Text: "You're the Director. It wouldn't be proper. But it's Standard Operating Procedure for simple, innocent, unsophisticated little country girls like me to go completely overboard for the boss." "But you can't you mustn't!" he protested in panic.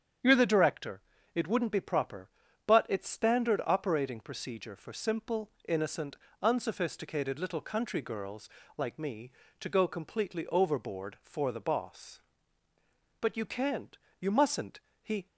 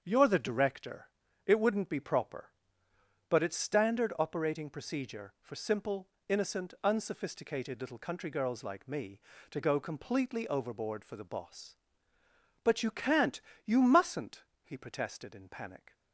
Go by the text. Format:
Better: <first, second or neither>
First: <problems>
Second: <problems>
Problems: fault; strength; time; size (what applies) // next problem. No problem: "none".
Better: second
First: starts louder than the rest; strong; until 1.5 s; 8 dB // pauses between "girls" and "like"; slight; at 8.4 s; 0.28 s long // pauses between "can't" and "you"; slight; at 13.9 s; 0.20 s long // stops before "protested in panic"; at 15.2 s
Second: starts louder than the rest; until 1.0 s; 7 dB // pauses between "can't" and "you"; slight; at 13.4 s; 0.22 s long